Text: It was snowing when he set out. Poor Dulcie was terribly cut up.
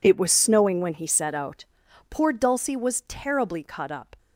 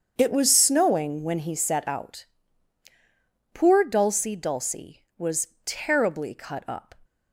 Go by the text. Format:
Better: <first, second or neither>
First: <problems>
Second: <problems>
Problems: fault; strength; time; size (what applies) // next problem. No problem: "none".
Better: first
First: none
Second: starts louder than the rest; strong; until 1.1 s; 7 dB // says "Dulcie" twice; at 4.3 s // pauses between "was" and "terribly"; slight; at 5.4 s; 0.16 s long